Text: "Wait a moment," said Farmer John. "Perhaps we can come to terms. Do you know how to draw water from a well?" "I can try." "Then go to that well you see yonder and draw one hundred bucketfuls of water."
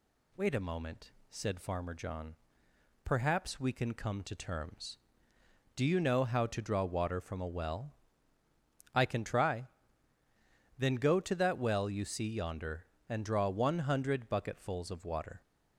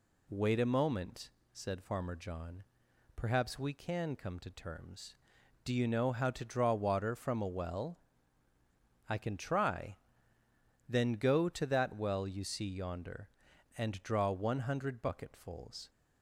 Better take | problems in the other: first | stops before "of water"; at 15.8 s

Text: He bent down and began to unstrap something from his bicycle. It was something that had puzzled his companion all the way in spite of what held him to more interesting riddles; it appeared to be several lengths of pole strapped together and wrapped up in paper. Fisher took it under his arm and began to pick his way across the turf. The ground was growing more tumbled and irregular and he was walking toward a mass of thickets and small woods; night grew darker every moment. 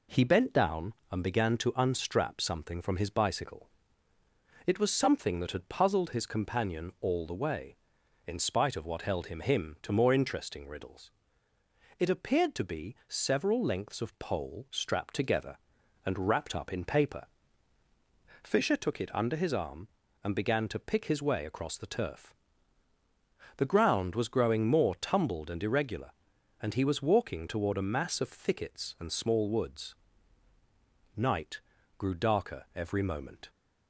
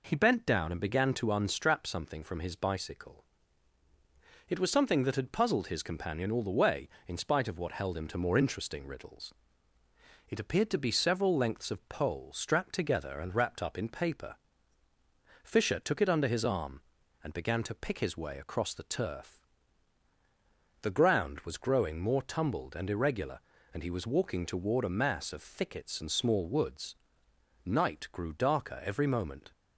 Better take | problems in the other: second | says "him" twice; at 9.3 s // pauses between "night" and "grew"; at 31.5 s; 0.38 s long

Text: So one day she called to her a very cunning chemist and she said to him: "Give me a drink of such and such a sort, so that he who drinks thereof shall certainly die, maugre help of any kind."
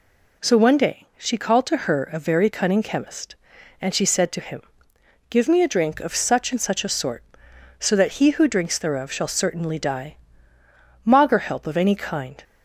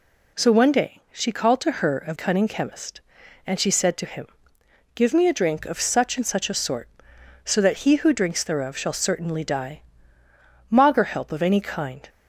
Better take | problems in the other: first | skips "very"; at 2.1 s

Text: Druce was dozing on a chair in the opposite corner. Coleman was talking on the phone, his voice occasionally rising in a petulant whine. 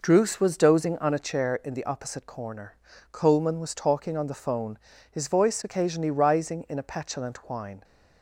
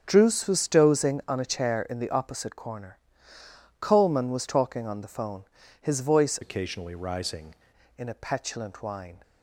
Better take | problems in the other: first | starts louder than the rest; until 1.0 s; 7 dB // changes voice from "occasionally" to "rising"; from 6.4 to 7.5 s; 1.1 s long

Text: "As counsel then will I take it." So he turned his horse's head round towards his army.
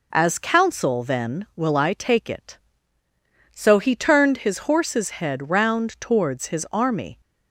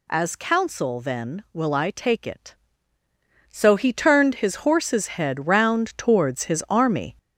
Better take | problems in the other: first | gets louder; noticeable; throughout; 4 dB

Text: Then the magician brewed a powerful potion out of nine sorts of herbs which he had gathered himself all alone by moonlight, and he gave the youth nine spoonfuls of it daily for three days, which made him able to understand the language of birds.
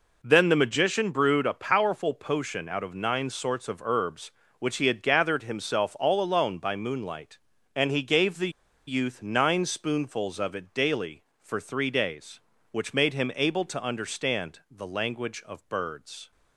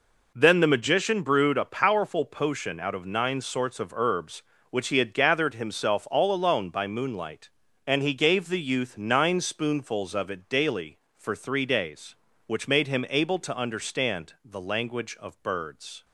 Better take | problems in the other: second | pauses between "the" and "youth"; at 8.4 s; 0.37 s long

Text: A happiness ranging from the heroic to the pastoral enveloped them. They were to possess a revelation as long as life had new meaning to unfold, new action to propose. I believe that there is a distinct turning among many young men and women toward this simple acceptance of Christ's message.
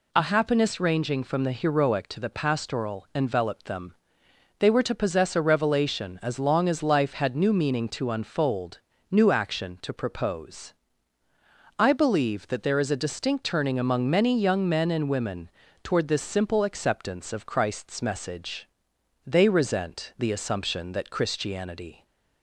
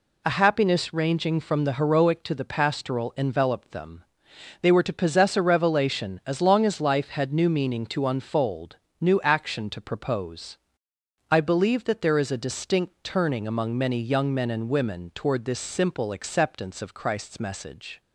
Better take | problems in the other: second | pauses between "women" and "toward"; slight; at 15.4 s; 0.36 s long // goes on to say "They resent the assumption that Christianity"; strong; from 19.2 s on; 2.8 s long

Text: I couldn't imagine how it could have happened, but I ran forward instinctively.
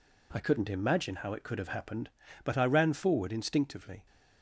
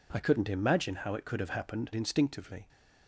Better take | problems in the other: first | skips "but I ran forward"; at 1.9 s

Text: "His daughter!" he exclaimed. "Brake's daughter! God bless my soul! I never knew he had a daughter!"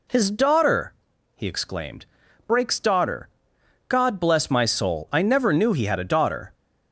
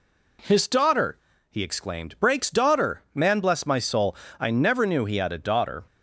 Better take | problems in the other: first | says "Man" for "God"; at 3.1 s

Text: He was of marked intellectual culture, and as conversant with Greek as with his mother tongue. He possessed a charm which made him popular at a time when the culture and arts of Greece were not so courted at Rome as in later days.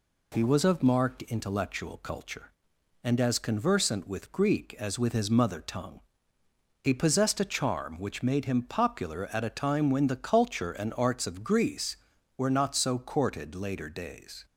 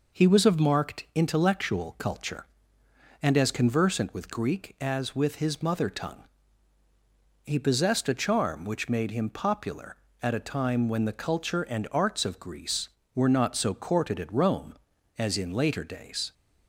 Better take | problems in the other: second | skips "at Rome as in"; at 13.5 s

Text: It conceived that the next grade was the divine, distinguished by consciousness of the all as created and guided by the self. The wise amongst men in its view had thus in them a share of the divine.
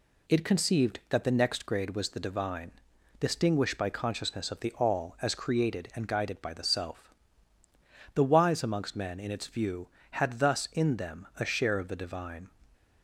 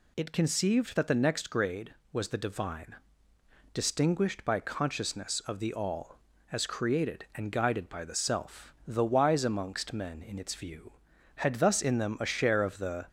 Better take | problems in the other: first | stops before "divine"; at 13.0 s

